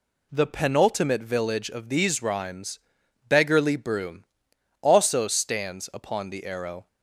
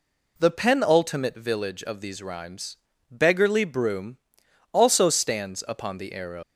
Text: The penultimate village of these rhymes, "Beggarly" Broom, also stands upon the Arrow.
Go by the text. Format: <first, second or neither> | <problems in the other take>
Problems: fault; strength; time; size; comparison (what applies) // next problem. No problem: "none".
first | leaves "Arrow" unfinished; at 6.4 s; 130 ms